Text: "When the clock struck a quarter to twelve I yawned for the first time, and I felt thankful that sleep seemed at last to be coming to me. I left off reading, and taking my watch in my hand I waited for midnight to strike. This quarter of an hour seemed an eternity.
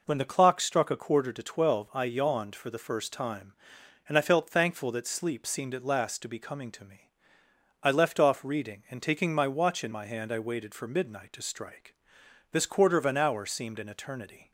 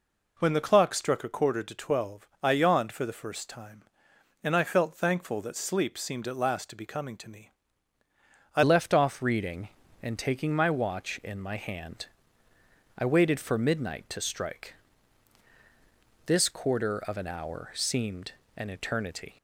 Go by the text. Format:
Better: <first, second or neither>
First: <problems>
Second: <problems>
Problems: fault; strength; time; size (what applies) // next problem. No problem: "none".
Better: first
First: none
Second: pauses between "twelve" and "I"; slight; at 2.2 s; 0.16 s long // changes voice at "left"; from 8.6 s on; 10.7 s long // pauses between "hand" and "I"; noticeable; at 12.0 s; 0.92 s long // pauses between "seemed" and "an"; slight; at 18.3 s; 0.26 s long